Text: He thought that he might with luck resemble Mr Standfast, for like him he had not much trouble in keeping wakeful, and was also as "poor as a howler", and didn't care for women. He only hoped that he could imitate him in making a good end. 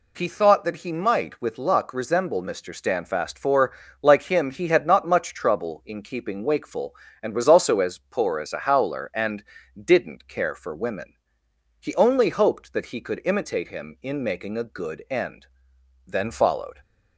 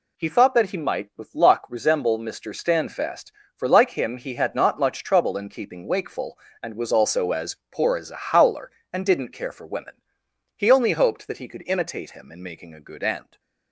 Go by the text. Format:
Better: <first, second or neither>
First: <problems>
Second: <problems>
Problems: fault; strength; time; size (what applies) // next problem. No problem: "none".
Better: second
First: pauses between "for" and "like"; slight; at 3.7 s; 0.28 s long // pauses between "and" and "didn't"; slight; at 9.4 s; 0.34 s long // goes on to say "Then followed"; noticeable; from 16.0 s on; 0.72 s long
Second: none